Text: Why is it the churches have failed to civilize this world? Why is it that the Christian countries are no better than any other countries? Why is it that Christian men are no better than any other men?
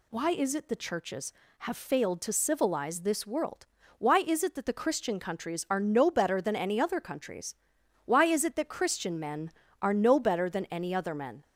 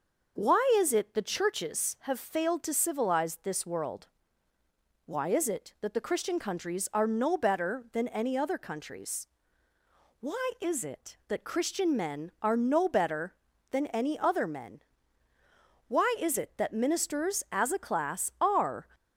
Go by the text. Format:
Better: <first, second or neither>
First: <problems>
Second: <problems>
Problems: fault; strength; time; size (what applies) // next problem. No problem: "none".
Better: first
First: none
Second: goes on to say "Why is it that ministers as a class are"; strong; from 15.8 s on; 2.9 s long